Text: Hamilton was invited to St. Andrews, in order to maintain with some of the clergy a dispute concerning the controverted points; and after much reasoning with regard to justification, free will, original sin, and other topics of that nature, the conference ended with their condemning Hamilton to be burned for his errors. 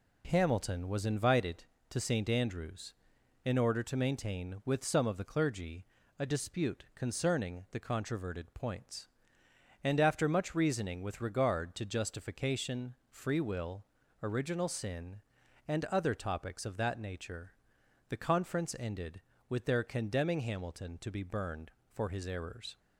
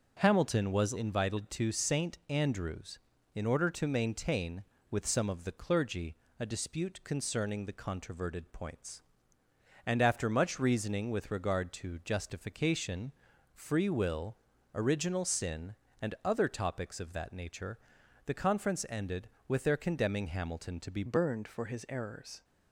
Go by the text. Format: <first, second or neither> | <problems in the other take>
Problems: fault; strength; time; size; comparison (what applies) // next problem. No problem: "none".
first | pauses between "clergy" and "a"; slight; at 6.1 s; 0.24 s long; slight in the first // changes voice at "burned"; from 21.0 s on; 1.4 s long